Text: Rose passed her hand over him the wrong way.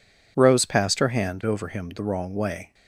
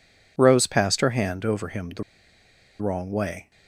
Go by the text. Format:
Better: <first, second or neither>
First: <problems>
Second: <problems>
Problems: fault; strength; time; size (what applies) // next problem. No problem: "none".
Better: first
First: none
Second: pauses between "the" and "wrong"; noticeable; at 2.0 s; 0.77 s long